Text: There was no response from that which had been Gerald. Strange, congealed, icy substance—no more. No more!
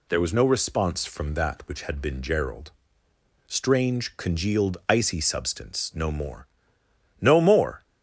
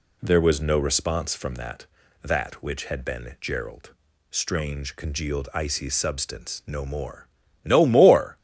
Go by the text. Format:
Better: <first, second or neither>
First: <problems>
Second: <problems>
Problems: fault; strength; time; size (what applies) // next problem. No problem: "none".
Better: first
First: none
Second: says "that" twice; at 2.2 s